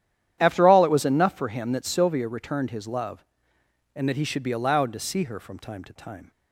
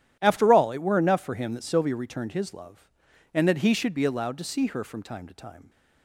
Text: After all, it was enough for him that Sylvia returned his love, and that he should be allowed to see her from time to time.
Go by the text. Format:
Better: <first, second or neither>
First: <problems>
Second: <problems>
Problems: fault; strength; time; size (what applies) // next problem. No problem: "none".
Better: first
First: starts louder than the rest; strong; until 1.4 s; 10.5 dB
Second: starts louder than the rest; strong; until 1.2 s; 10.5 dB // says "were" for "was"; at 0.8 s